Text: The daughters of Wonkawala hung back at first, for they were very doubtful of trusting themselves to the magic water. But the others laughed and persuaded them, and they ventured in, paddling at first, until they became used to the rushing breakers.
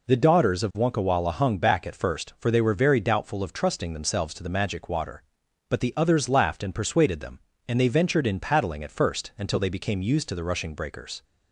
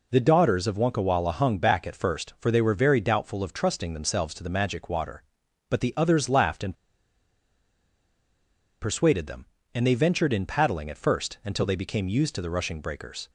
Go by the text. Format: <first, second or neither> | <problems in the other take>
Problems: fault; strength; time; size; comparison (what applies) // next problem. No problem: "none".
first | pauses between "and" and "persuaded"; strong; at 6.7 s; 2.0 s long